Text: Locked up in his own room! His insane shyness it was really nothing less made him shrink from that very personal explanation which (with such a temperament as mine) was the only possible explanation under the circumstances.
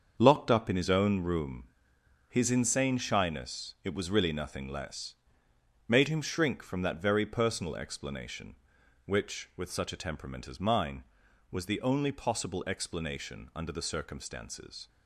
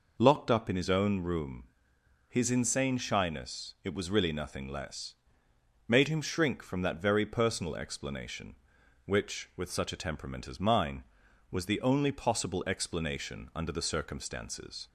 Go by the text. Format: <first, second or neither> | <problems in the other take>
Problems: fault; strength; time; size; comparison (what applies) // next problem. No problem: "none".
second | gets quieter; strong; throughout; 9 dB // pauses between "less" and "made"; noticeable; at 5.1 s; 0.74 s long; noticeable in the second